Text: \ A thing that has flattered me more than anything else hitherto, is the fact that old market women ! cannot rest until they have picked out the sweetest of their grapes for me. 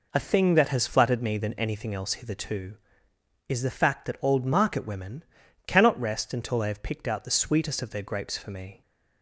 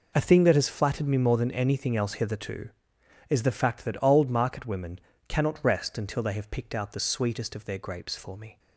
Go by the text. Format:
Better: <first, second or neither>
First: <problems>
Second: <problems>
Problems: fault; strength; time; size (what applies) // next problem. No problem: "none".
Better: second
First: skips "more"; at 1.3 s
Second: none